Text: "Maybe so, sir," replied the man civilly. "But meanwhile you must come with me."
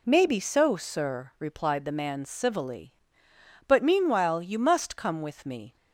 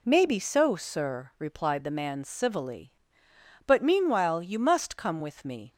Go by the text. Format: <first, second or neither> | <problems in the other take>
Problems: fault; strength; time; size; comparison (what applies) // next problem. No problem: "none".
neither | none